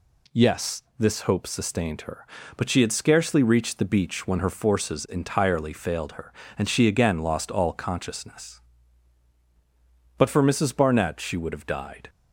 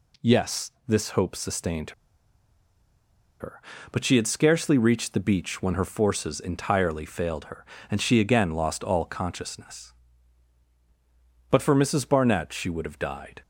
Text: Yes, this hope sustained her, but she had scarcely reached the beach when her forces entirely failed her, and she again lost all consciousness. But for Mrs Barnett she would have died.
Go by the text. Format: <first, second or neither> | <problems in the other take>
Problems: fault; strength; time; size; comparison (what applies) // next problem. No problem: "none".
first | pauses between "sustained" and "her"; strong; at 1.9 s; 1.4 s long